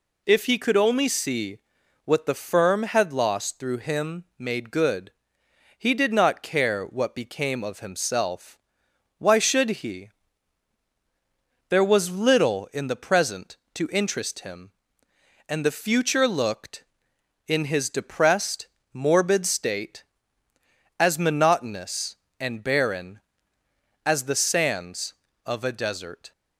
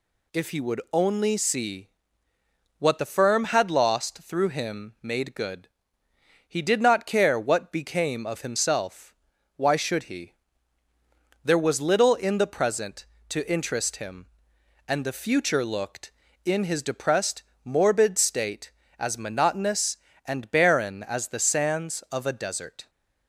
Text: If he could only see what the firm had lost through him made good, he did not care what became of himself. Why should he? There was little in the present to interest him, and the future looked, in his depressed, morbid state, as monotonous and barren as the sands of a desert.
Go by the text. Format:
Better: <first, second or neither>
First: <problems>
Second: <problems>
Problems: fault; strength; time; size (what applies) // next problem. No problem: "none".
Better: first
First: pauses between "see" and "what"; noticeable; at 1.5 s; 0.46 s long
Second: says "would" for "could"; at 0.5 s // pauses between "see" and "what"; noticeable; at 1.8 s; 0.90 s long